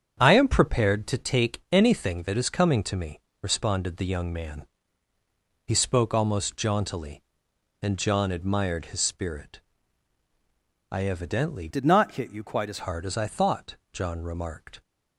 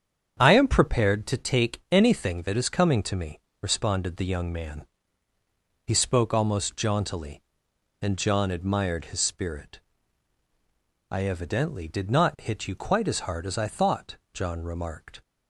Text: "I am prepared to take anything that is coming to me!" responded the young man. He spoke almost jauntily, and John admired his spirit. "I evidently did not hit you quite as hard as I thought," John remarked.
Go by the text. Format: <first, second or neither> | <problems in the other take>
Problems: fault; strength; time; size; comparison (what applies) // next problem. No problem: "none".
second | starts louder than the rest; strong; until 1.2 s; 8 dB; strong in the second // changes voice from "did" to "as"; from 11.6 to 12.7 s; 1.1 s long